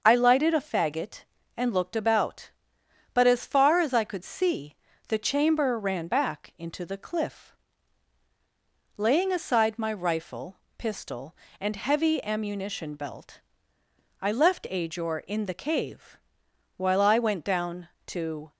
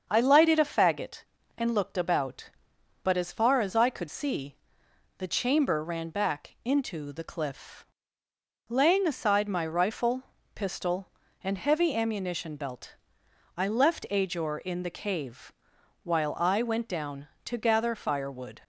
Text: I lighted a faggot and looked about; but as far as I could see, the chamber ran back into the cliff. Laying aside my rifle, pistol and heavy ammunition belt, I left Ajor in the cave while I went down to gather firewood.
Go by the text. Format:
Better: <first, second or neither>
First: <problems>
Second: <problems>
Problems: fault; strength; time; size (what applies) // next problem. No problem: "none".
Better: second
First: starts louder than the rest; until 1.0 s; 6.5 dB // pauses between "cave" and "while"; noticeable; at 16.1 s; 0.58 s long // stops before "gather firewood"; at 18.5 s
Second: starts louder than the rest; until 1.1 s; 7 dB // pauses between "cave" and "while"; noticeable; at 15.5 s; 0.52 s long